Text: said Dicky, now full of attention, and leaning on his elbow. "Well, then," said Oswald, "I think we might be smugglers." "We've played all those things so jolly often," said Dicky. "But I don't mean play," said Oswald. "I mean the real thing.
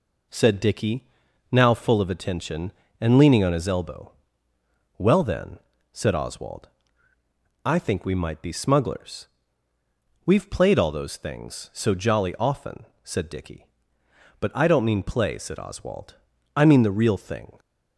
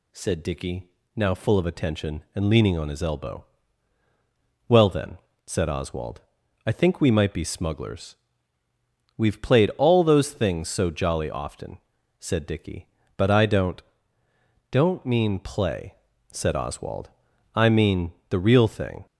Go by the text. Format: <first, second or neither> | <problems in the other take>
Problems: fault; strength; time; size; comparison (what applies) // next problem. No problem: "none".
first | says "don't" twice; at 14.7 s // pauses between "mean" and "the"; slight; at 18.1 s; 0.18 s long